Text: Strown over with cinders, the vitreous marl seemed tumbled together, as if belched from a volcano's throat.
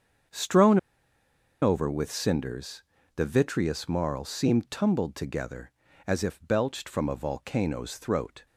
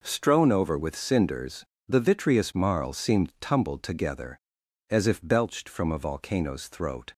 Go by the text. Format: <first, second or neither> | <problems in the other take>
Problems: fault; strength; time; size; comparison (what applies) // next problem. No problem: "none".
second | starts louder than the rest; strong; until 2.1 s; 7 dB // pauses between "Strown" and "over"; noticeable; at 0.7 s; 0.84 s long